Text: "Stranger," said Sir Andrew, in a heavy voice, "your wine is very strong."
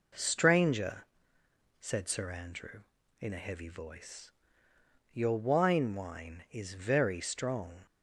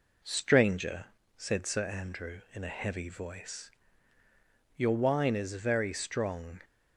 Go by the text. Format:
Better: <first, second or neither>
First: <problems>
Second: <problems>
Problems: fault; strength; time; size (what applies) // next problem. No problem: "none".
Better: second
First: says "wine" twice; at 5.9 s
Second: none